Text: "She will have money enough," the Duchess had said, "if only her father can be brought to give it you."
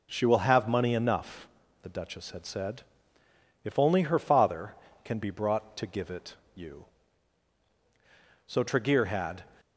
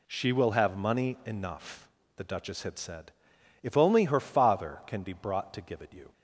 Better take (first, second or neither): second